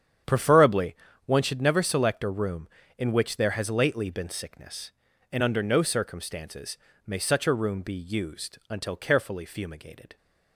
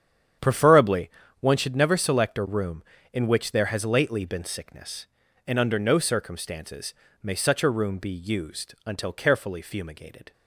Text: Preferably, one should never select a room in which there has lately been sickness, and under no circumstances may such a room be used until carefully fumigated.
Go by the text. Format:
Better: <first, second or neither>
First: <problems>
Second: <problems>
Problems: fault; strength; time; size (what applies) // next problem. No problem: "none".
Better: neither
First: starts louder than the rest; strong; until 1.5 s; 8.5 dB // pauses between "circumstances" and "may"; slight; at 6.7 s; 0.28 s long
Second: starts louder than the rest; strong; until 1.7 s; 8.5 dB // pauses between "circumstances" and "may"; slight; at 6.9 s; 0.28 s long